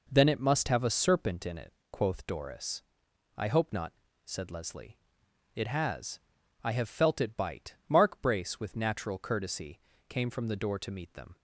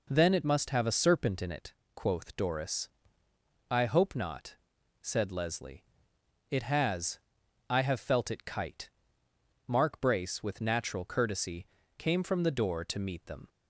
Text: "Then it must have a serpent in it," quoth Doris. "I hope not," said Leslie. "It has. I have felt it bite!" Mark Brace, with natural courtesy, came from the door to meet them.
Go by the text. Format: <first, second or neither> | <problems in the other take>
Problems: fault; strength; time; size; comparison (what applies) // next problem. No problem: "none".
first | says "kite" for "bite"; at 8.4 s